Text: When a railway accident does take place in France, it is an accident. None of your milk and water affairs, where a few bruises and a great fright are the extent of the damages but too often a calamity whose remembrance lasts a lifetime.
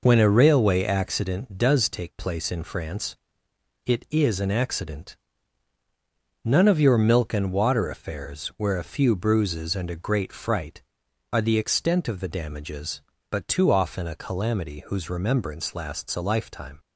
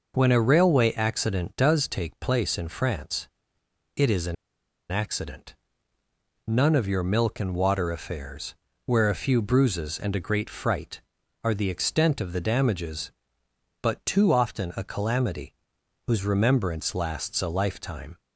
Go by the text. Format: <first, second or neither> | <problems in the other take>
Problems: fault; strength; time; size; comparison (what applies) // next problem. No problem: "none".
first | pauses between "an" and "accident"; noticeable; at 4.3 s; 0.56 s long // pauses between "calamity" and "whose"; noticeable; at 15.5 s; 0.52 s long